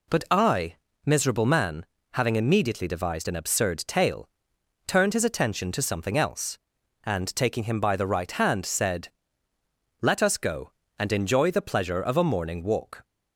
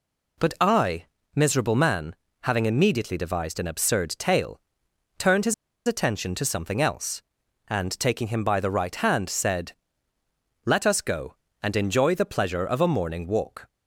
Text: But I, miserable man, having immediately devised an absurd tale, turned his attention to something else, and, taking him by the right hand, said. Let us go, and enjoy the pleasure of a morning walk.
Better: first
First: none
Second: pauses between "his" and "attention"; slight; at 5.5 s; 0.32 s long

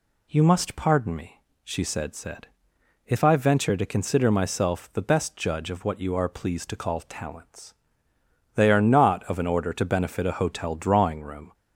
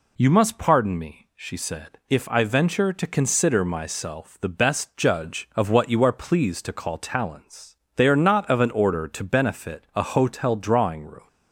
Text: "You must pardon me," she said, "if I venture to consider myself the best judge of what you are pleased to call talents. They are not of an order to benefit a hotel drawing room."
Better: second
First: says "said" twice; at 2.1 s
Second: none

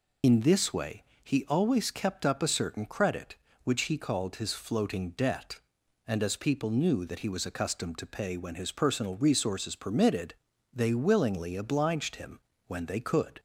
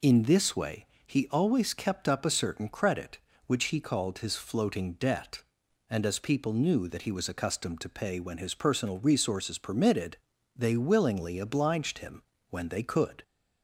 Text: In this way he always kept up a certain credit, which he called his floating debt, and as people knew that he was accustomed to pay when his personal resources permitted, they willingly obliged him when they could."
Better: second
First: loses the start of "In"; at 0.2 s; 45 ms // pauses between "way" and "he"; slight; at 1.0 s; 0.20 s long // pauses between "him" and "when"; slight; at 12.3 s; 0.28 s long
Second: pauses between "way" and "he"; slight; at 0.8 s; 0.20 s long // pauses between "him" and "when"; slight; at 12.2 s; 0.28 s long

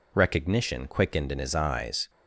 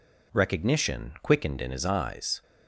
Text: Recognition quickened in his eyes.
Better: neither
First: none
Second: none

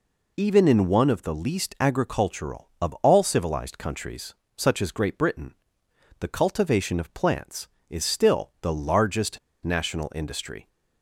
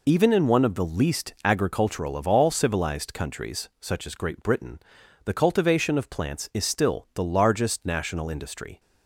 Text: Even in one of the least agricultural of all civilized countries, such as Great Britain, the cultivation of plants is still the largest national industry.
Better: second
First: pauses between "largest" and "national"; slight; at 9.3 s; 0.25 s long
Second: none

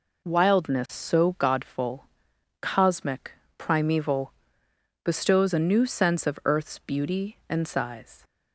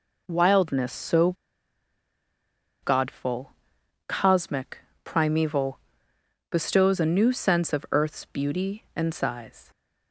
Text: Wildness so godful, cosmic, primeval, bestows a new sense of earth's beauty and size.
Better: first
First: none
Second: pauses between "so" and "godful"; strong; at 1.3 s; 1.5 s long

